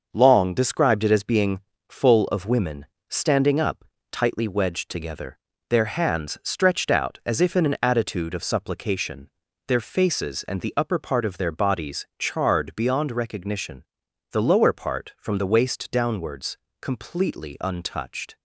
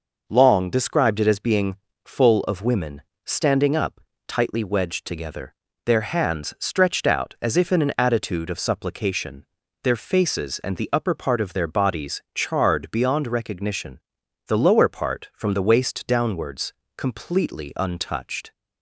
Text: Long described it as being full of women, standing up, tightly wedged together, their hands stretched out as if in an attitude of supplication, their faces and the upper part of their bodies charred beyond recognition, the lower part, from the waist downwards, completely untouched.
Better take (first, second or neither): second